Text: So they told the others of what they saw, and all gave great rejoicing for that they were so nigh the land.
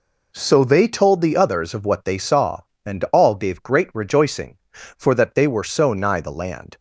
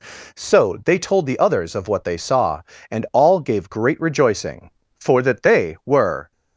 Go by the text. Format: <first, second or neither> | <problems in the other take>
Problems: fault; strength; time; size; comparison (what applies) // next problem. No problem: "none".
first | stops before "so nigh the land"; at 6.3 s